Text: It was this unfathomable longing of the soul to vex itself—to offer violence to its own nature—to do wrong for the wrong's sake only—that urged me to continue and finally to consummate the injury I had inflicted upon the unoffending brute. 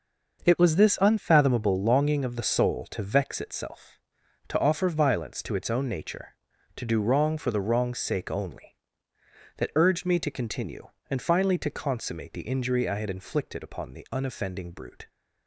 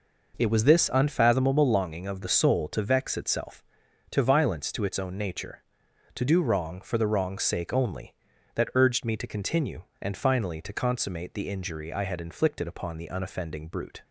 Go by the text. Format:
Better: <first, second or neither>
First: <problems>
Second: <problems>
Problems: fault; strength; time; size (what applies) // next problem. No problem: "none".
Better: first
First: none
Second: skips "offer"; at 4.2 s